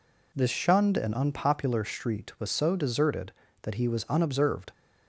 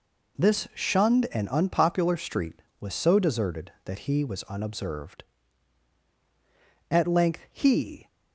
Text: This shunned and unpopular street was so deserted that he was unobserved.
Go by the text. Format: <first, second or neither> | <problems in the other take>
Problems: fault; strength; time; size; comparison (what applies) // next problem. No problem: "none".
first | goes on to say "At length he"; noticeable; from 6.9 s on; 1.1 s long